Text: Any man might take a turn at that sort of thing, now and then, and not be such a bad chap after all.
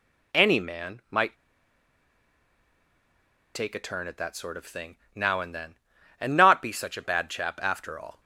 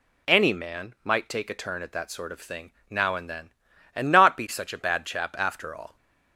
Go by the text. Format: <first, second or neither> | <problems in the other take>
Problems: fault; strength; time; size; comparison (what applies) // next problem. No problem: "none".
second | pauses between "might" and "take"; strong; at 1.3 s; 2.2 s long